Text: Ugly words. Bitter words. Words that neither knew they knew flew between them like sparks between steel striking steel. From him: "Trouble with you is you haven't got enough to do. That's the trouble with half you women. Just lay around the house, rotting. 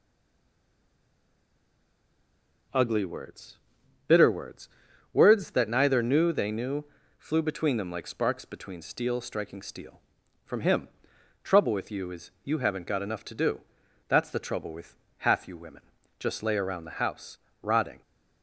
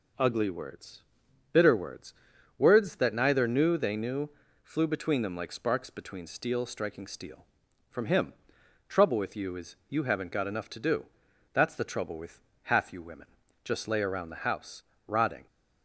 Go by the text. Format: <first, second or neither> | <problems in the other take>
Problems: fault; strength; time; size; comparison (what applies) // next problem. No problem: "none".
second | stays silent before the first word; strong; until 2.7 s; 2.7 s long // pauses between "knew" and "flew"; slight; at 6.8 s; 0.32 s long; slight in the second // pauses between "with" and "half"; slight; at 14.9 s; 0.22 s long; slight in the second